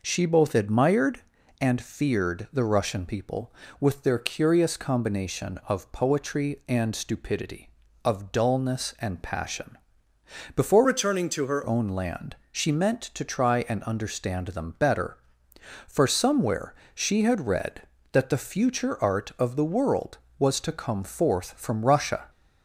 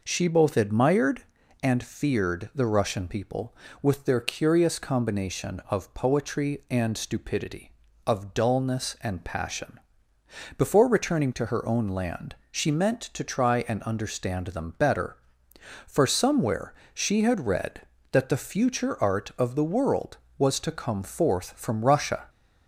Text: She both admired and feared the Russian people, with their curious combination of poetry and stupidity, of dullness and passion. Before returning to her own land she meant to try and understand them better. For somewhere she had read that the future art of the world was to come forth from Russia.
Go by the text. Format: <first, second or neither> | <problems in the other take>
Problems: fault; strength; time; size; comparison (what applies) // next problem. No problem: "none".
second | changes voice from "returning" to "her"; from 10.8 to 11.6 s; 0.8 s long // pauses between "land" and "she"; slight; at 12.3 s; 0.16 s long; slight in the second // pauses between "somewhere" and "she"; slight; at 16.7 s; 0.20 s long; slight in the second